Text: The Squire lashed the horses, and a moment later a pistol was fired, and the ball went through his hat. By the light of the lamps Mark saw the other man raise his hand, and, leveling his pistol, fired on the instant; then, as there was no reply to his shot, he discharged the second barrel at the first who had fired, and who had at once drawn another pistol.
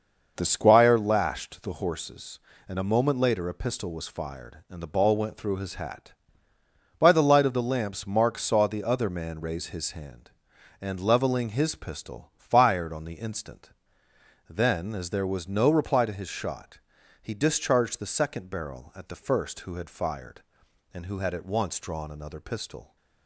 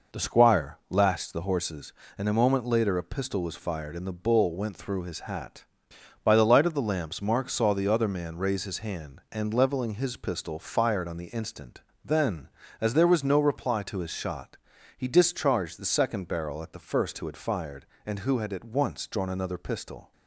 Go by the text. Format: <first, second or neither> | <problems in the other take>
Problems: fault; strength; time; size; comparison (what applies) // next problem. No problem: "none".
first | says "bull" for "ball"; at 4.1 s